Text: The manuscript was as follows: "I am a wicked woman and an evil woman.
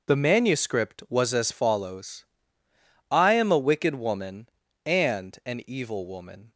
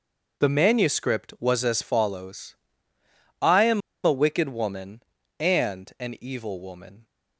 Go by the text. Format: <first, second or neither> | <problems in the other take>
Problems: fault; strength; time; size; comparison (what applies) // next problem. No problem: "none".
first | pauses between "am" and "a"; slight; at 3.8 s; 0.26 s long